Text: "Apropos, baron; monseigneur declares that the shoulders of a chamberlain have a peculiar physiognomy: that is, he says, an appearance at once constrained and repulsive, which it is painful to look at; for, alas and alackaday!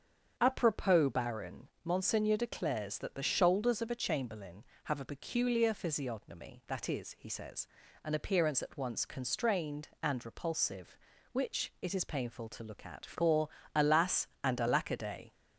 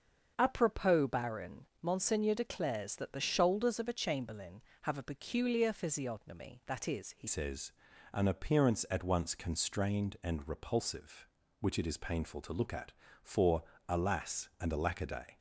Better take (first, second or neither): first